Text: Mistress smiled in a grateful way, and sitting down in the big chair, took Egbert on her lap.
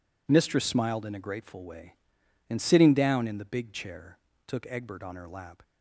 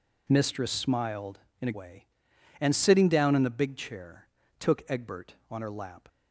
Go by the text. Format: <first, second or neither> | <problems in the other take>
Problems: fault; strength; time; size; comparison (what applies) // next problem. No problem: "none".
first | skips "grateful"; at 1.7 s